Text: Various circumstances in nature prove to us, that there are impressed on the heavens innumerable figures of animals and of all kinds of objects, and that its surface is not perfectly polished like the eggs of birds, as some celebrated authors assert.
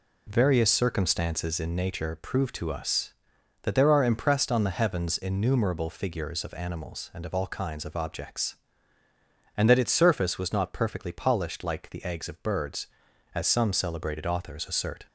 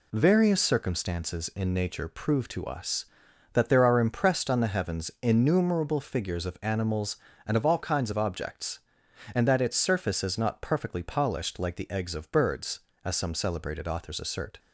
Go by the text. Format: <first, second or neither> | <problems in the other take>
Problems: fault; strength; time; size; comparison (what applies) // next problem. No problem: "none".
second | says "was" for "is"; at 10.3 s